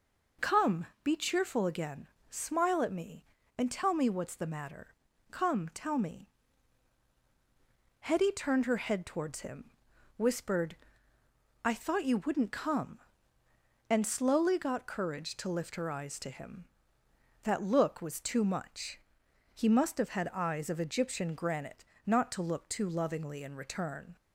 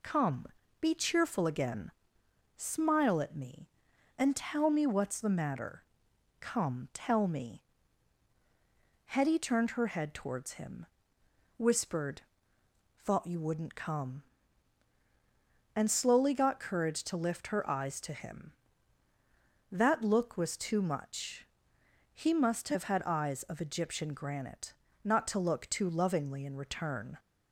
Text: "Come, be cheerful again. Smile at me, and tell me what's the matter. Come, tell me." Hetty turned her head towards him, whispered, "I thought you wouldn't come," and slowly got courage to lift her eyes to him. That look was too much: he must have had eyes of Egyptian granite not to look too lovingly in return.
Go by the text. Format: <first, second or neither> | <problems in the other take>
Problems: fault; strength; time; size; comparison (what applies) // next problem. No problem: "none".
first | skips "I"; at 12.5 s // pauses between "granite" and "not"; slight; at 24.7 s; 0.32 s long; slight in the first